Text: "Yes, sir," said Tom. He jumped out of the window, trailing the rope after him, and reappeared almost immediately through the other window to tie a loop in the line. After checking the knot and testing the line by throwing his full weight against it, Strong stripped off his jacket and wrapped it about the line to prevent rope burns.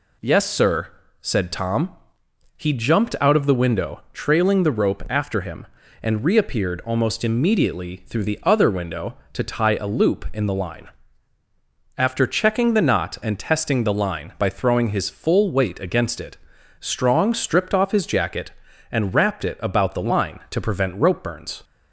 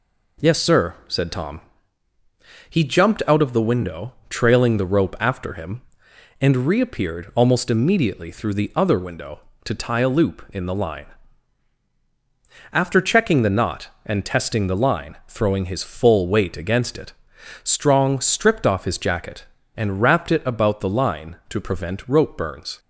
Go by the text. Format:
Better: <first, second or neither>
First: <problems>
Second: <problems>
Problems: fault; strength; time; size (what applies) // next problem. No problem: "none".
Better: first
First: none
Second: skips "by"; at 15.2 s